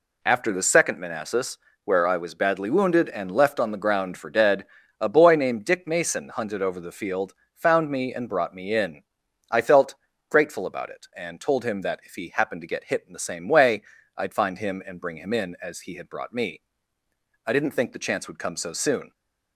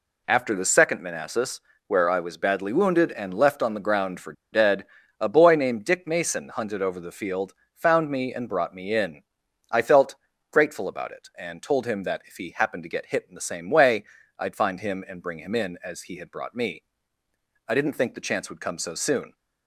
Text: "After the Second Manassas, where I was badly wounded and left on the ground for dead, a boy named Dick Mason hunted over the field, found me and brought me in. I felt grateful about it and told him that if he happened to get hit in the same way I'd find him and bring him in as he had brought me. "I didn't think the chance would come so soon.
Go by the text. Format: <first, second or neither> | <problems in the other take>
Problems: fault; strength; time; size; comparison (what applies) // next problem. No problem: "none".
first | pauses between "for" and "dead"; slight; at 4.3 s; 0.20 s long // pauses between "felt" and "grateful"; slight; at 10.1 s; 0.36 s long; slight in the first // pauses between "way" and "I'd"; slight; at 14.0 s; 0.34 s long; slight in the first